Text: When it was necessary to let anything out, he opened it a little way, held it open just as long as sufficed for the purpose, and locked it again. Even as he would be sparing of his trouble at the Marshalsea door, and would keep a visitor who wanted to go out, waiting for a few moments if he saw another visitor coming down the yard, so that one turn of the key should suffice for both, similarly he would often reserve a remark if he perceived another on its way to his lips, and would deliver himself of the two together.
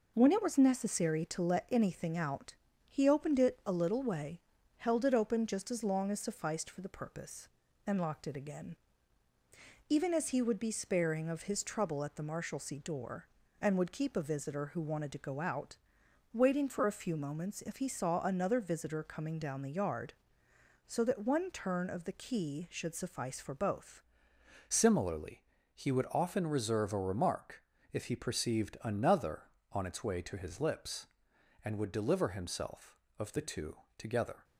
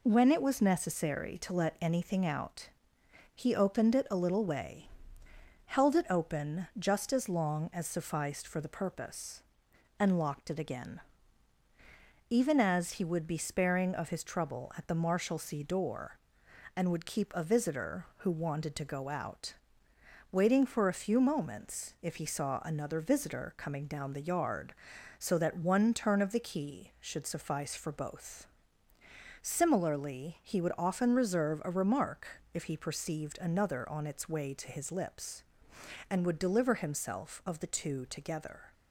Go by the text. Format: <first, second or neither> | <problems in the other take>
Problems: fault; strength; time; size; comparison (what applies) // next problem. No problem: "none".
second | changes voice at "similarly"; from 24.6 s on; 9.8 s long // pauses between "similarly" and "he"; slight; at 25.3 s; 0.36 s long // pauses between "remark" and "if"; slight; at 27.6 s; 0.28 s long; slight in the second // pauses between "two" and "together"; slight; at 33.7 s; 0.22 s long